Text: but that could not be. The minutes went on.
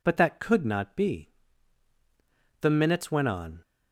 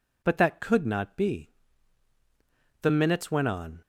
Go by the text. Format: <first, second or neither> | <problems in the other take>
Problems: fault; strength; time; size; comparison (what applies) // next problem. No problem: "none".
neither | none